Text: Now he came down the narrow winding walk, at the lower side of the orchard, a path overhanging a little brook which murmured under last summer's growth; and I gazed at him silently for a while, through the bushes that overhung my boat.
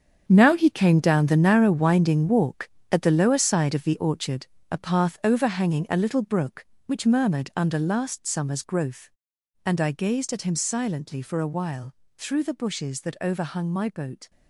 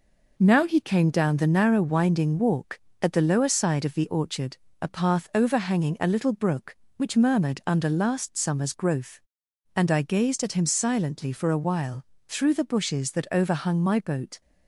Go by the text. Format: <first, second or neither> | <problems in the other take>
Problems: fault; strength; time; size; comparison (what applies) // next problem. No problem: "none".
second | gets quieter; strong; throughout; 11.5 dB